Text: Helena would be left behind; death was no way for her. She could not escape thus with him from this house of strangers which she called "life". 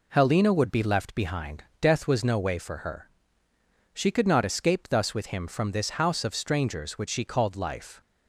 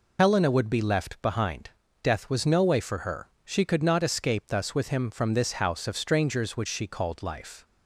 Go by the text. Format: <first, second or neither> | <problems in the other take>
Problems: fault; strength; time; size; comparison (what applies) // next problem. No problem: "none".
first | loses the start of "Helena"; at 0.1 s; 65 ms